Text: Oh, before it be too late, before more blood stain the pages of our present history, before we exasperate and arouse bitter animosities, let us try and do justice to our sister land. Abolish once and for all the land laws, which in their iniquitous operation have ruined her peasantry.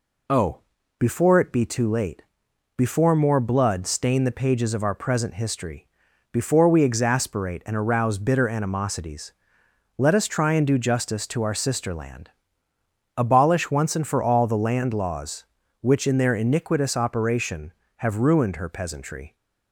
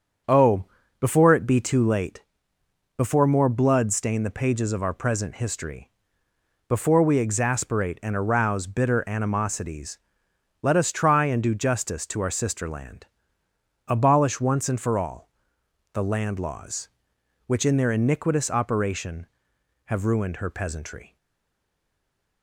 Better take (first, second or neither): first